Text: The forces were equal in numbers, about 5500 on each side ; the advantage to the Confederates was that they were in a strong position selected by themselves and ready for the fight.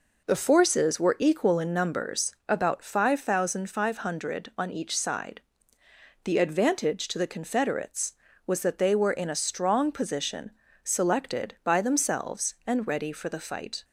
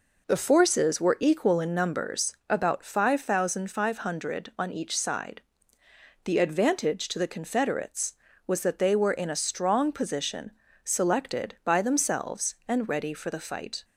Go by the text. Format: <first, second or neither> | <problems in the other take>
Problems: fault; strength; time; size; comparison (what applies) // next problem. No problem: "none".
neither | pauses between "position" and "selected"; slight; the same in both